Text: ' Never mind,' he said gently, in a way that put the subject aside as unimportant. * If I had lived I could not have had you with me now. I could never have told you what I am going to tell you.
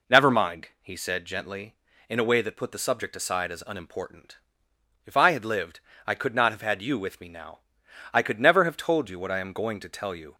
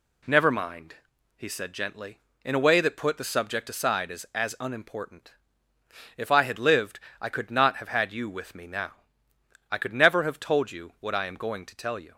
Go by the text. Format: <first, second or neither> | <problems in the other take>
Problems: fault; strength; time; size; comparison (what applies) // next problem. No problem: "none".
first | says "as" twice; at 4.3 s // pauses between "lived" and "I"; slight; at 6.9 s; 0.22 s long; slight in the first